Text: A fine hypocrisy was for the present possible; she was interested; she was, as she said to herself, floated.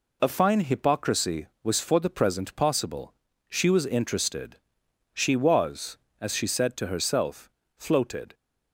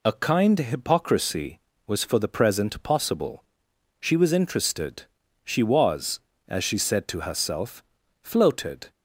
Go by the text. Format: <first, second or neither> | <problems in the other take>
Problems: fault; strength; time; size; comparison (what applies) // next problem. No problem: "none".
first | says "kind" for "fine"; at 0.1 s